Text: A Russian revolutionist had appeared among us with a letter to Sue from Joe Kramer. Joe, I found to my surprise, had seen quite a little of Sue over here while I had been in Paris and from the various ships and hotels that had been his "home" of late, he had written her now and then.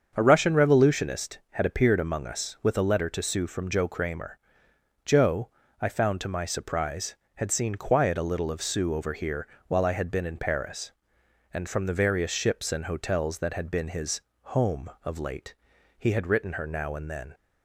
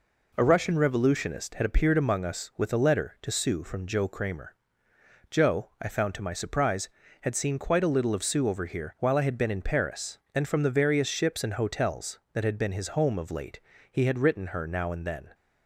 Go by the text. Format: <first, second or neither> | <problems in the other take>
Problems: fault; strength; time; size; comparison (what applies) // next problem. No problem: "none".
second | starts louder than the rest; until 1.1 s; 7 dB // says "quiet" for "quite"; at 7.7 s // pauses between "here" and "while"; slight; at 9.4 s; 0.18 s long // pauses between "his" and "home"; slight; at 14.1 s; 0.22 s long